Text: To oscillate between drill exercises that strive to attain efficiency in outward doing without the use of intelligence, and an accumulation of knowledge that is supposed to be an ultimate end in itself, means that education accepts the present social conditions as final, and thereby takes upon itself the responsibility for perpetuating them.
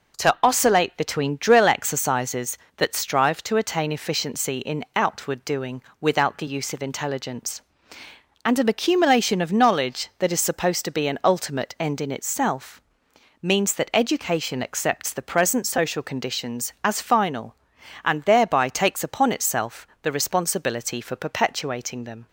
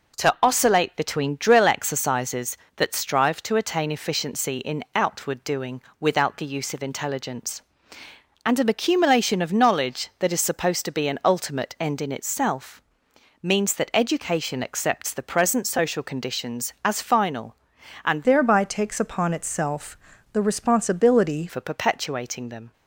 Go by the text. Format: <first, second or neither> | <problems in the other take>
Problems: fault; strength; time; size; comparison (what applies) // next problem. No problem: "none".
first | pauses between "doing" and "without"; slight; at 5.8 s; 0.18 s long; slight in the first // changes voice from "thereby" to "responsibility"; from 18.2 to 21.4 s; 3.2 s long // pauses between "itself" and "the"; slight; at 19.9 s; 0.36 s long; slight in the first